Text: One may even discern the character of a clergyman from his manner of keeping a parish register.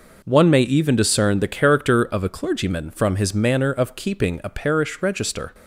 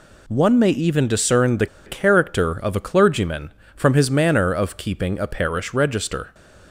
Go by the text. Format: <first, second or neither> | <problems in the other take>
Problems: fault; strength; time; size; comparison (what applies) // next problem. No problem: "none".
first | pauses between "the" and "character"; slight; at 1.6 s; 0.19 s long